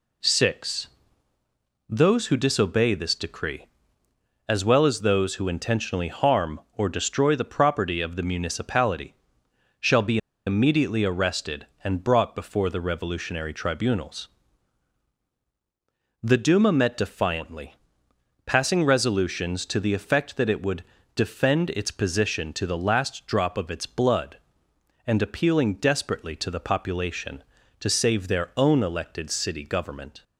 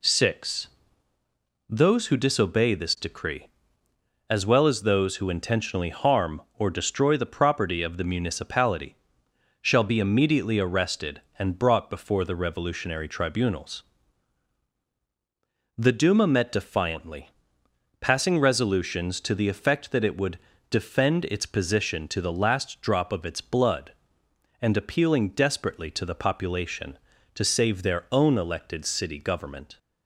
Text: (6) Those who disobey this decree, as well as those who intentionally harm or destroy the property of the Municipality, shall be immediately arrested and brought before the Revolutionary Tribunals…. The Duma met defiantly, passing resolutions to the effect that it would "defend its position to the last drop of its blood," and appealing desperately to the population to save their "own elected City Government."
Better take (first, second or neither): second